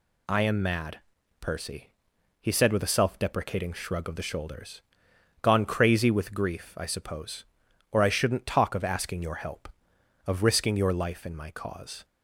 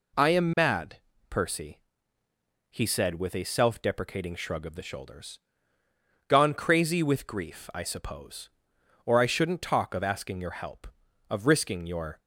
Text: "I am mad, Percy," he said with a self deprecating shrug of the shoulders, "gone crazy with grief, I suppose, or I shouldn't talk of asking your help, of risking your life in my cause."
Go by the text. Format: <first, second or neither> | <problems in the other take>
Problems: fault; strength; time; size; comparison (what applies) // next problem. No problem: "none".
first | stops before "life in my cause"; at 12.1 s